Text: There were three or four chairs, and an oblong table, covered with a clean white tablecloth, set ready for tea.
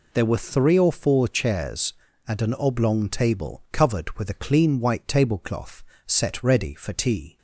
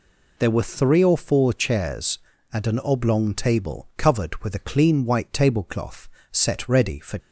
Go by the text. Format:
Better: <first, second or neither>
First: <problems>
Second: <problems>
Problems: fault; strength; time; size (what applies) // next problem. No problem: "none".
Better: first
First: none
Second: stops before "tea"; at 7.1 s